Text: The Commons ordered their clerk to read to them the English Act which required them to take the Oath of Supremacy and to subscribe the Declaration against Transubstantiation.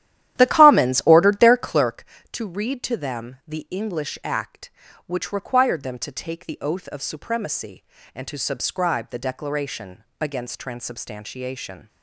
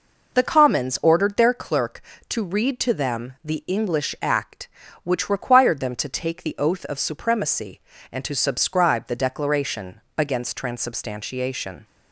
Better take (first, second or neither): second